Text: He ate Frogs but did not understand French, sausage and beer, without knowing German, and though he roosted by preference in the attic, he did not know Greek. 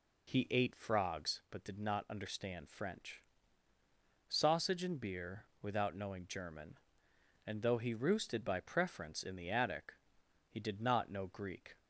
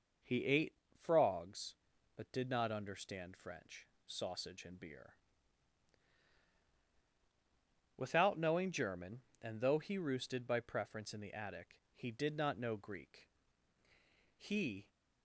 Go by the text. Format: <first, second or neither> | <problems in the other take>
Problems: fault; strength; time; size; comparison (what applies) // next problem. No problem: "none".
first | pauses between "ate" and "Frogs"; slight; at 0.7 s; 0.22 s long // goes on to say "He"; from 14.3 s on; 0.52 s long